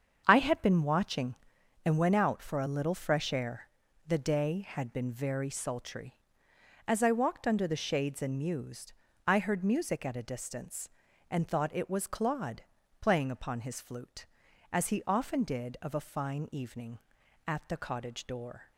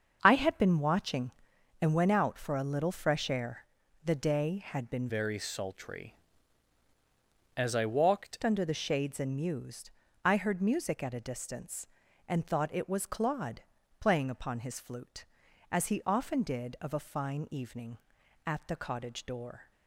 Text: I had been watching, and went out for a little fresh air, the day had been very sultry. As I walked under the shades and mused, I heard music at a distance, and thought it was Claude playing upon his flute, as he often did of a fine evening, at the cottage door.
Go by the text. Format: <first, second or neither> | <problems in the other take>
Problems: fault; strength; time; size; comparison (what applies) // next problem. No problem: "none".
first | starts louder than the rest; until 1.2 s; 7 dB; strong in the first // changes voice from "very" to "walked"; from 5.0 to 8.3 s; 3.3 s long // pauses between "Claude" and "playing"; at 13.6 s; 0.40 s long; also in the first